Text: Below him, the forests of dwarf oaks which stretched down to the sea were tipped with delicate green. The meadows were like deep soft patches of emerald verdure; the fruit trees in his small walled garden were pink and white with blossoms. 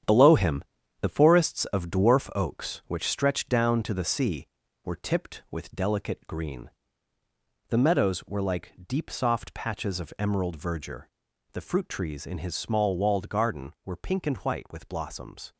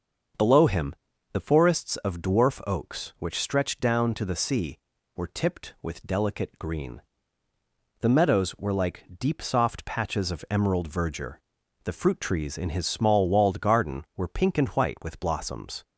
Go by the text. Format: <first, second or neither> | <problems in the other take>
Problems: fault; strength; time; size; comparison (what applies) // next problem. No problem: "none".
second | gets quieter; strong; throughout; 7.5 dB // starts louder than the rest; strong; until 1.4 s; 9 dB; also in the second